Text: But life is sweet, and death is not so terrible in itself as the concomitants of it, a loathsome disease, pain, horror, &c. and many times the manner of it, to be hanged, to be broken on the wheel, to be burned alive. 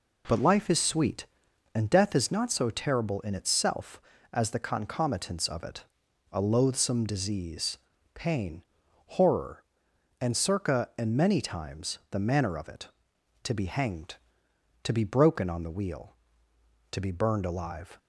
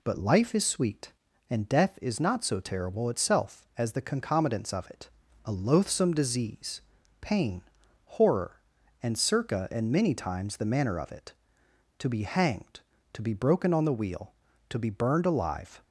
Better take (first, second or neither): first